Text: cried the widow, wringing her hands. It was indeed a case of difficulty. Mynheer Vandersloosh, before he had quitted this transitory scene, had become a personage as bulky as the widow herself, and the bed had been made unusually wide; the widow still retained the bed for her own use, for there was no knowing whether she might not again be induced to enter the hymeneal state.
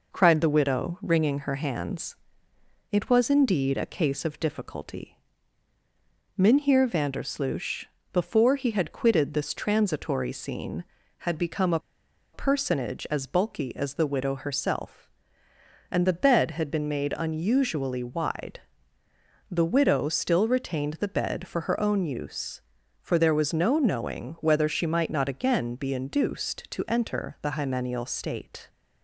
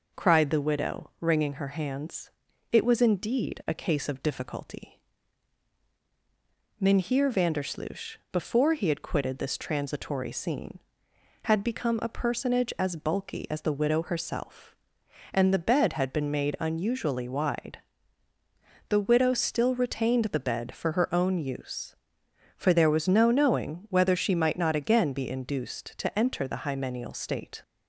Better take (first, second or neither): second